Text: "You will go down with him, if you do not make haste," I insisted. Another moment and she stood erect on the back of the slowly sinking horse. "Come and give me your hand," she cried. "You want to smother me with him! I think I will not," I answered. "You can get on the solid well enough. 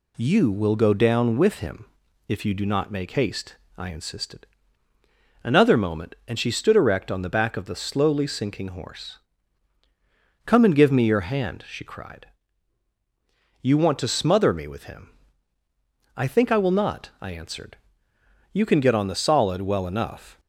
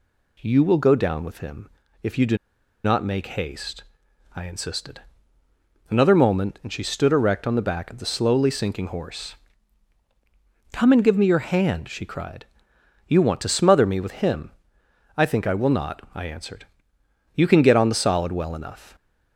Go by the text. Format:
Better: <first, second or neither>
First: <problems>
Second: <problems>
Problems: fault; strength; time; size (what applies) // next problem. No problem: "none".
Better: first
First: none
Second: pauses between "do" and "not"; noticeable; at 2.3 s; 0.48 s long